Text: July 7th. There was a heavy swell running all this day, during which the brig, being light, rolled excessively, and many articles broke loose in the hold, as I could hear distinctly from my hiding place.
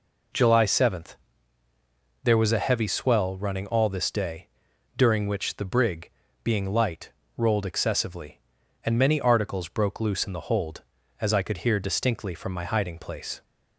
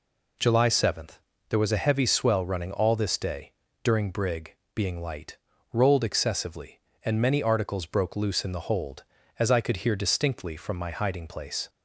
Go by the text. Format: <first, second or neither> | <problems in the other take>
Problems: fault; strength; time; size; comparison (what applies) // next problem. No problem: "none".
first | skips "which the"; at 4.1 s